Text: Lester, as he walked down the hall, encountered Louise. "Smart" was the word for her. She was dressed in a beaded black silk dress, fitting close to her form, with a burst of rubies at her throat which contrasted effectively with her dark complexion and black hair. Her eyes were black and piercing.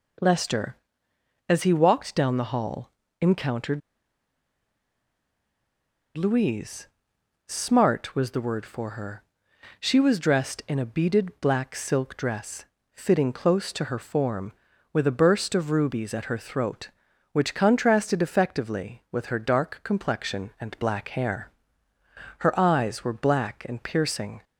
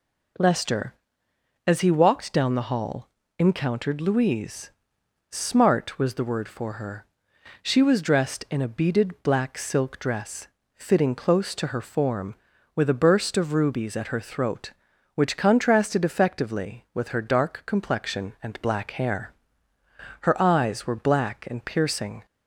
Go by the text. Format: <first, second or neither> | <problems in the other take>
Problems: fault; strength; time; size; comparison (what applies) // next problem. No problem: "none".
second | pauses between "encountered" and "Louise"; strong; at 3.8 s; 2.3 s long